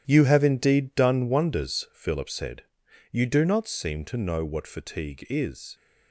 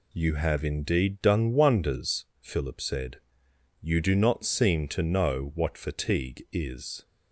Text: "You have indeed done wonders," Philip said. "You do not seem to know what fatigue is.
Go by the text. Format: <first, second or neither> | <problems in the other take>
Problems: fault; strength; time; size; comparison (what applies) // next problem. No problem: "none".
second | gets quieter; strong; throughout; 10.5 dB